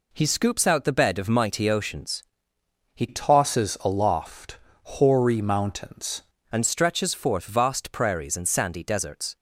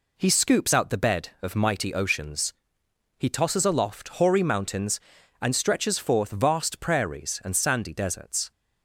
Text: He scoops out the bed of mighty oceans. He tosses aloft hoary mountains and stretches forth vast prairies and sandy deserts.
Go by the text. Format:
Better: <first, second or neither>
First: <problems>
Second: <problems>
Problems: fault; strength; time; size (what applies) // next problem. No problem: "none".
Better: second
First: changes voice from "tosses" to "mountains"; from 3.0 to 6.2 s; 3.2 s long // pauses between "aloft" and "hoary"; slight; at 4.5 s; 0.28 s long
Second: none